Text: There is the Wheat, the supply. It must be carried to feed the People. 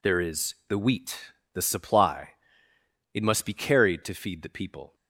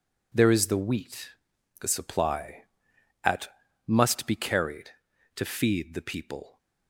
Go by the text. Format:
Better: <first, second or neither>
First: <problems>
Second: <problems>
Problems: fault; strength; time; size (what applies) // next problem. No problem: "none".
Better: first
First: none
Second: says "At" for "It"; at 3.2 s